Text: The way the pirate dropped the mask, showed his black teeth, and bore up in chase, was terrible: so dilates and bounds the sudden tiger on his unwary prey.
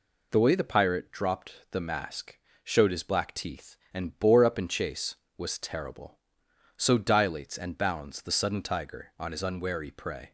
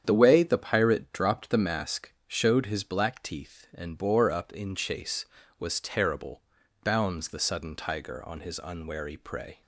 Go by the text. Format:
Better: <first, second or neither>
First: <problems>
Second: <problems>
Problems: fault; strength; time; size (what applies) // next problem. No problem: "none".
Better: first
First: none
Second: starts louder than the rest; strong; until 1.0 s; 8.5 dB // skips "so dilates and"; at 6.6 s